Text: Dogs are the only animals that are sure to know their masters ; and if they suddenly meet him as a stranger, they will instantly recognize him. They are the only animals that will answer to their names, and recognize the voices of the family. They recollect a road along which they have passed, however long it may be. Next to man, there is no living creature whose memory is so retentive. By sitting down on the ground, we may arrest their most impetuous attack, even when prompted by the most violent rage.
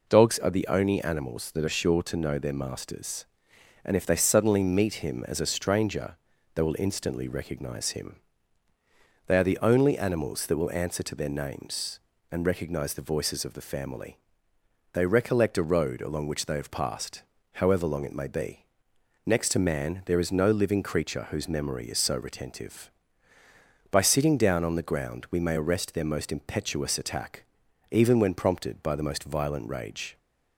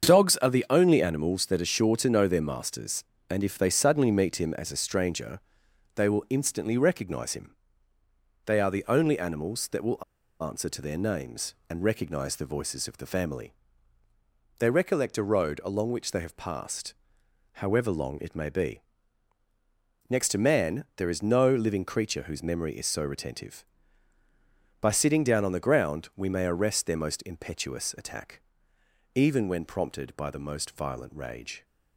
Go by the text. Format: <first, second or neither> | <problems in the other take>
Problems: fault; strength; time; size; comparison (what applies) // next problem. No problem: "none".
first | starts louder than the rest; until 1.1 s; 7 dB // pauses between "will" and "answer"; at 10.0 s; 0.39 s long